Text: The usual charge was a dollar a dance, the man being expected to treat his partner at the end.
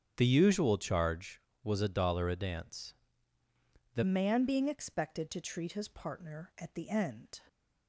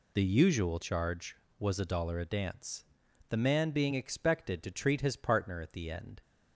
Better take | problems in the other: second | starts louder than the rest; strong; until 1.1 s; 8.5 dB // changes voice at "man"; from 4.0 s on; 3.3 s long

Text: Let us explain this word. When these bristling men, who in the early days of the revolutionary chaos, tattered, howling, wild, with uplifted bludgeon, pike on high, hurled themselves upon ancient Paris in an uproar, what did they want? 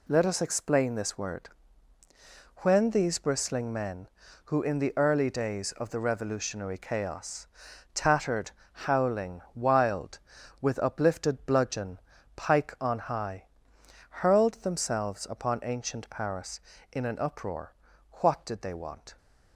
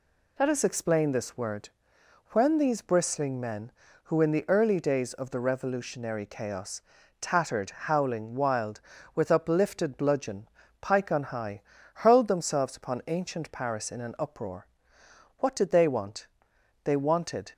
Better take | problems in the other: first | goes on to say "They wanted"; noticeable; from 16.8 s on; 0.68 s long

